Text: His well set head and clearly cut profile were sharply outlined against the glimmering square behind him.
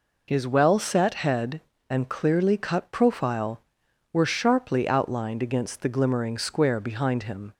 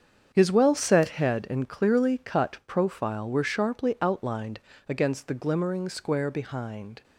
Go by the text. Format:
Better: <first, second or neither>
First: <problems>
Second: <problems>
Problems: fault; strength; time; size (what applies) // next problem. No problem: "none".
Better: first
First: none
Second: starts louder than the rest; strong; until 1.3 s; 7.5 dB // pauses between "outlined" and "against"; slight; at 4.5 s; 0.30 s long // stops before "him"; at 7.0 s